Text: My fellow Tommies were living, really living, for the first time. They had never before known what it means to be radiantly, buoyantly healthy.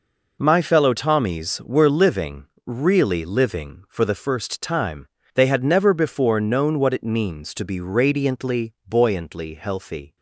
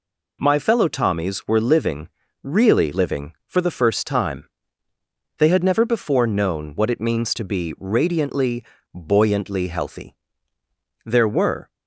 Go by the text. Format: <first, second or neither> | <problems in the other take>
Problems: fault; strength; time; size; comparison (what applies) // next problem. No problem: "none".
first | goes on to say "There were"; noticeable; from 11.0 s on; 0.64 s long